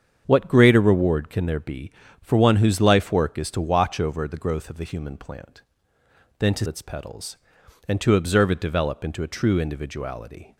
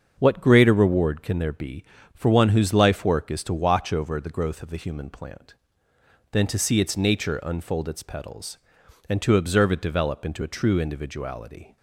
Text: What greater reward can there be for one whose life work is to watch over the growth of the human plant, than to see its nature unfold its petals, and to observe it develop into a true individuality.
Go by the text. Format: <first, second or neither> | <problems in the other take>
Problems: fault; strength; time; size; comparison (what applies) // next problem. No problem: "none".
second | starts louder than the rest; strong; until 1.2 s; 7.5 dB; also in the second // skips "see its nature unfold"; at 6.6 s